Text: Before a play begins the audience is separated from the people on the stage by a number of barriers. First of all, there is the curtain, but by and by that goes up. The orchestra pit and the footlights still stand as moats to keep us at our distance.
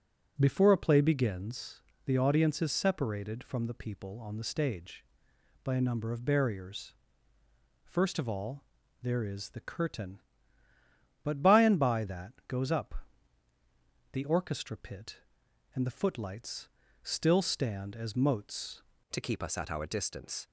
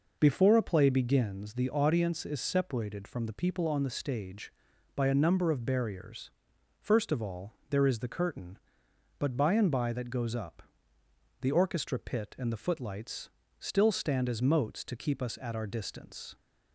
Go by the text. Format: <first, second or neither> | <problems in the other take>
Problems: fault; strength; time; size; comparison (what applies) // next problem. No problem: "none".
second | pauses between "begins" and "the"; slight; at 1.8 s; 0.24 s long // pauses between "footlights" and "still"; slight; at 16.6 s; 0.34 s long; slight in the second // changes voice at "to"; from 19.0 s on; 1.4 s long